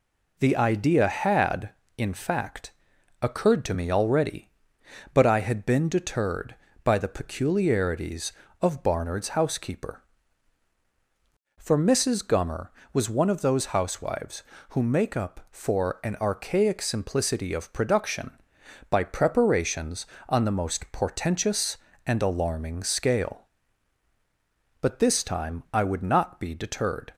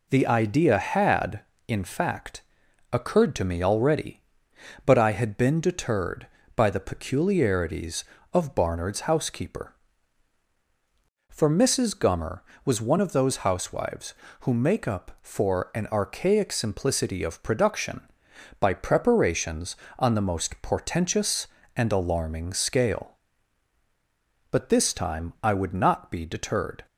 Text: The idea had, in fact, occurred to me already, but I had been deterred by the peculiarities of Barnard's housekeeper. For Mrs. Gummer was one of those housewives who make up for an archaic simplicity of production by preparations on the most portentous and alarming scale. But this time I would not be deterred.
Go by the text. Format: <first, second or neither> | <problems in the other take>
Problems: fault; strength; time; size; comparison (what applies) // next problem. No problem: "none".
neither | none